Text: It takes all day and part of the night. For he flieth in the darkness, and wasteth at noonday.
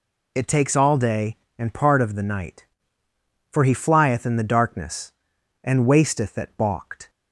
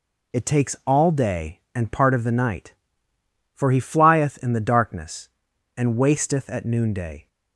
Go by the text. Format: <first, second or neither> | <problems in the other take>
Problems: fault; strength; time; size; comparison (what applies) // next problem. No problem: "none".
second | says "balked" for "noonday"; at 6.5 s